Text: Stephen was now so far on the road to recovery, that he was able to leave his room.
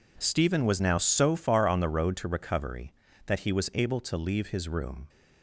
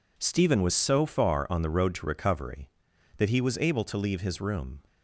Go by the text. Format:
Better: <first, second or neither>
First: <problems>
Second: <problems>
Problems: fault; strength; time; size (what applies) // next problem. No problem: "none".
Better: first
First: none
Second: skips "now"; at 0.7 s